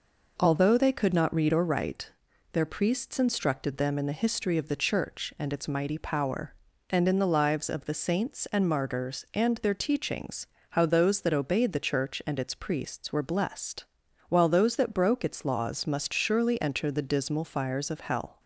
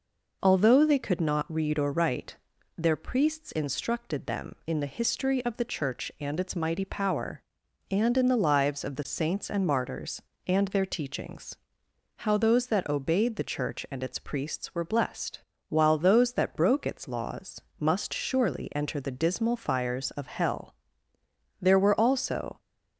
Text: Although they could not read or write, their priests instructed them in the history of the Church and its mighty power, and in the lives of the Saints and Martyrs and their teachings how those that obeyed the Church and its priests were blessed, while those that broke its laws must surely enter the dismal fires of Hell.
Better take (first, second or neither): first